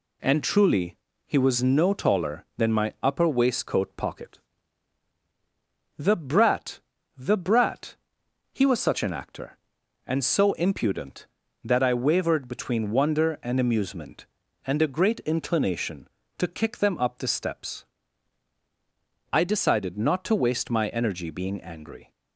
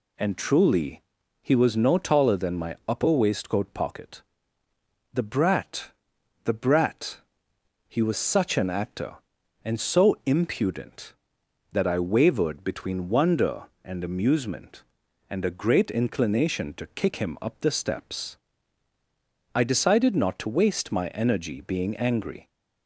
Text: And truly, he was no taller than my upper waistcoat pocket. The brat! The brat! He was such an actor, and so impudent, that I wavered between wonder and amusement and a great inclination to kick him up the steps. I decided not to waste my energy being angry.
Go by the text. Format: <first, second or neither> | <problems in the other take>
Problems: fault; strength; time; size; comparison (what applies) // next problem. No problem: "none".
second | says "them" for "him"; at 16.7 s